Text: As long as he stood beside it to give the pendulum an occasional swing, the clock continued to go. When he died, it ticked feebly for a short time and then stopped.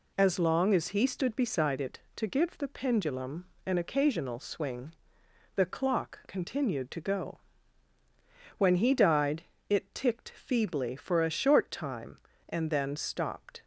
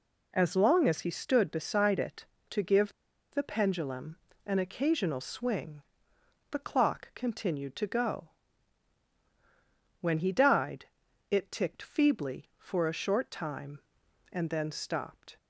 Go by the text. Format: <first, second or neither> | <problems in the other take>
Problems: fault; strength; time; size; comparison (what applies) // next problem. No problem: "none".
first | pauses between "give" and "the"; at 2.9 s; 0.40 s long // pauses between "pendulum" and "an"; slight; at 4.1 s; 0.30 s long; slight in the first